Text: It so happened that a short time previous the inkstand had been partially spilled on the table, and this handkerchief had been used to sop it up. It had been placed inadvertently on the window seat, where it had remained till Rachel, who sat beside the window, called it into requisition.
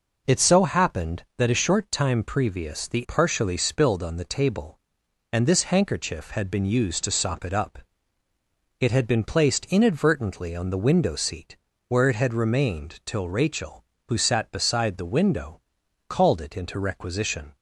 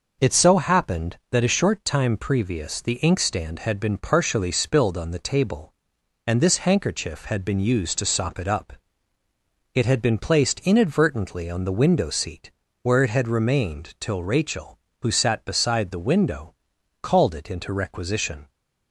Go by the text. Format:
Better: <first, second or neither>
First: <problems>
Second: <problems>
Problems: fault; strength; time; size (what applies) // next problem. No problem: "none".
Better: second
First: skips "inkstand had been"; at 3.0 s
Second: none